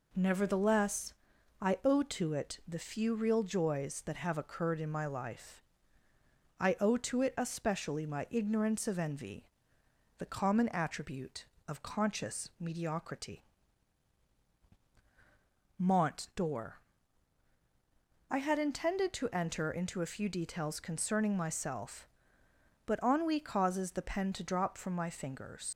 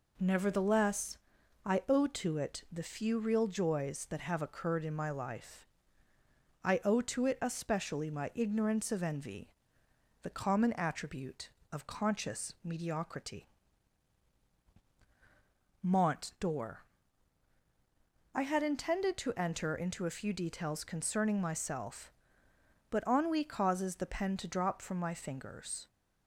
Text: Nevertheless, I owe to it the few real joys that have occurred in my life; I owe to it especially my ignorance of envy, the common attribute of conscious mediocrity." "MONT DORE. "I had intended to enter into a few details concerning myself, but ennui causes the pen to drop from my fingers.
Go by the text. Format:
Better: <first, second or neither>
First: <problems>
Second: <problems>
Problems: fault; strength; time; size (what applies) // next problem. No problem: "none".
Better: second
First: leaves "fingers" unfinished; at 25.7 s; 110 ms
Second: none